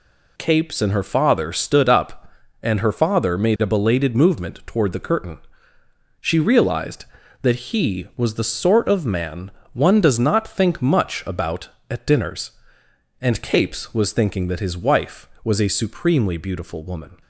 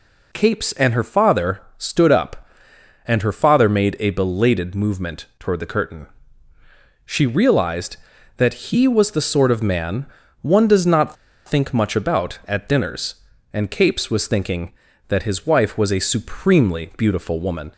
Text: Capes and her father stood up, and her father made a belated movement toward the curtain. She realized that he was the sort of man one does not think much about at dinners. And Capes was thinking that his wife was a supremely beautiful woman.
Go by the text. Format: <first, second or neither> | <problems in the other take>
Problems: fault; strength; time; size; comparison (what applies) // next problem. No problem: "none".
first | pauses between "father" and "stood"; slight; at 1.6 s; 0.16 s long // pauses between "man" and "one"; slight; at 10.0 s; 0.36 s long; slight in the first // pauses between "not" and "think"; slight; at 11.1 s; 0.32 s long